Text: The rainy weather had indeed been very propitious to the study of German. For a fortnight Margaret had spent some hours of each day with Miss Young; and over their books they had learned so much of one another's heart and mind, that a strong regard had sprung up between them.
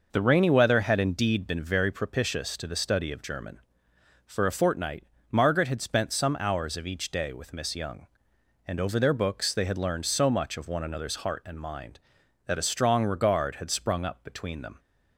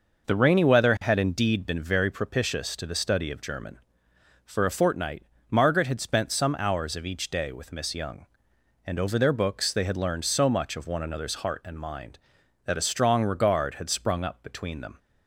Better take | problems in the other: neither | pauses between "fortnight" and "Margaret"; slight; the same in both

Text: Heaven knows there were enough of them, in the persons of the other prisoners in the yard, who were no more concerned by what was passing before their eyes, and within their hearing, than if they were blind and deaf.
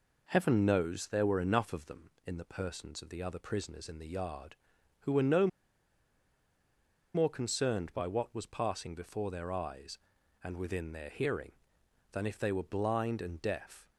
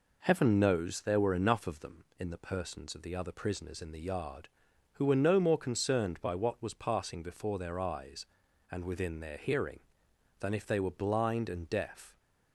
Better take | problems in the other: second | pauses between "no" and "more"; strong; at 5.4 s; 1.6 s long

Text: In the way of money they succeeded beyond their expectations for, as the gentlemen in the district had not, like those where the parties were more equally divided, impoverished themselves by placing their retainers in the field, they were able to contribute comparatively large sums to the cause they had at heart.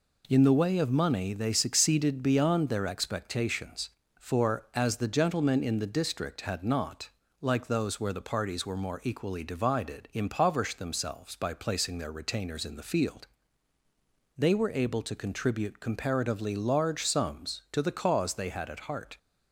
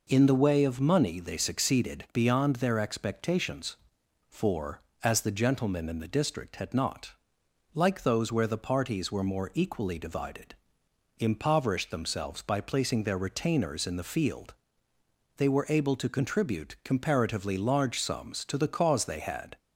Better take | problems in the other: first | stops before "at heart"; at 19.5 s

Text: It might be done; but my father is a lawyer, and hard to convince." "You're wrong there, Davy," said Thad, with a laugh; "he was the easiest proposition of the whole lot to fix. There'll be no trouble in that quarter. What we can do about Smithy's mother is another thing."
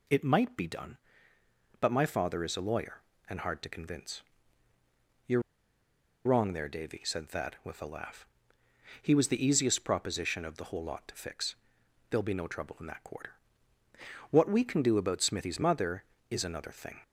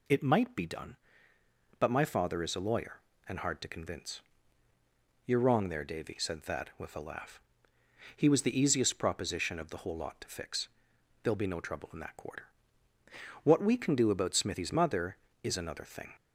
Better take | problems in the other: second | pauses between "You're" and "wrong"; noticeable; at 5.4 s; 0.84 s long

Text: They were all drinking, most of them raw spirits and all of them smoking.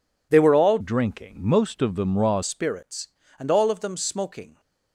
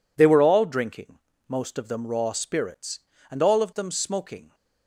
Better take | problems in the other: second | changes voice from "drinking" to "raw"; from 0.7 to 2.4 s; 1.7 s long

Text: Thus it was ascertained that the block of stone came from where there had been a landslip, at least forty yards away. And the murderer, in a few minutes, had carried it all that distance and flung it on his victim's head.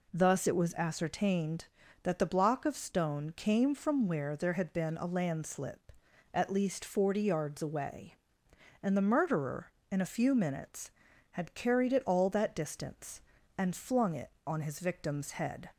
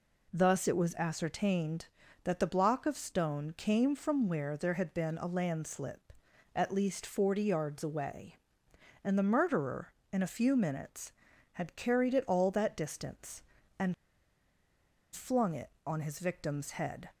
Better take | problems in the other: first | pauses between "and" and "flung"; at 13.9 s; 1.1 s long

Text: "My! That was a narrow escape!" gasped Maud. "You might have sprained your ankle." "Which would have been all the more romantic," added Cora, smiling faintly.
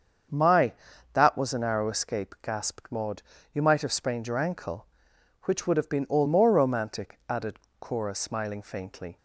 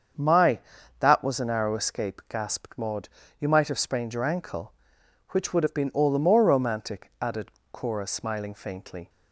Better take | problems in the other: second | starts louder than the rest; until 1.7 s; 7 dB; also in the second // skips "the"; at 6.2 s // pauses between "added" and "Cora"; slight; at 7.5 s; 0.22 s long; slight in the second

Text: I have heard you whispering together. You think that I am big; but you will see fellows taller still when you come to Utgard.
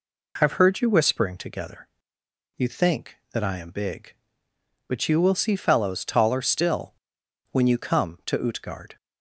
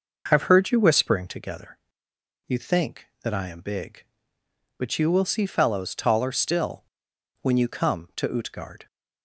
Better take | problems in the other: first | starts louder than the rest; noticeable; until 1.4 s; 5.5 dB // pauses between "still" and "when"; noticeable; at 6.8 s; 0.60 s long; noticeable in the first

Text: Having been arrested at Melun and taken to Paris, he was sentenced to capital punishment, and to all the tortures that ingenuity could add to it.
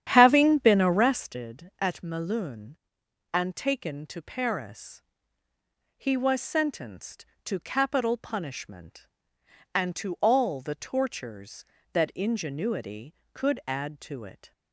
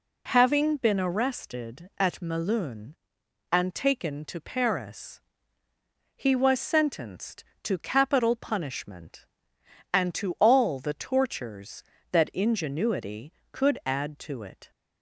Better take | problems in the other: second | starts louder than the rest; strong; until 1.4 s; 10 dB

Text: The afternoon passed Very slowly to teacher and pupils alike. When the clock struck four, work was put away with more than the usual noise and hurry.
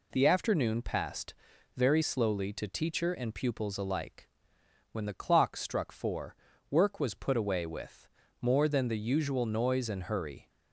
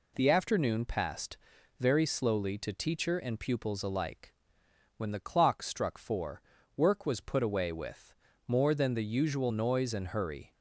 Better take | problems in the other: neither | pauses between "passed" and "Very"; the same in both // pauses between "with" and "more"; slight; the same in both

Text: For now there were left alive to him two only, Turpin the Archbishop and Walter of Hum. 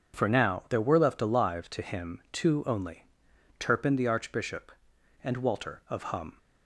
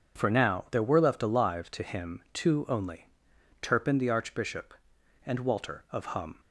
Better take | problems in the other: neither | none

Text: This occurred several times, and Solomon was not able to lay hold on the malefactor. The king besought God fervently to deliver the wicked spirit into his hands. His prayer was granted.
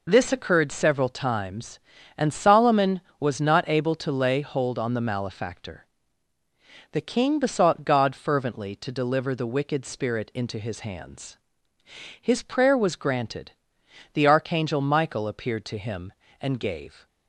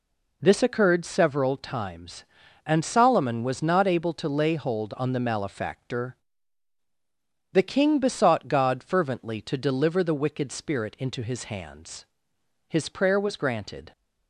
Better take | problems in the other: second | goes on to say "The archangel Michael appeared to him and gave"; strong; from 14.1 s on; 2.9 s long

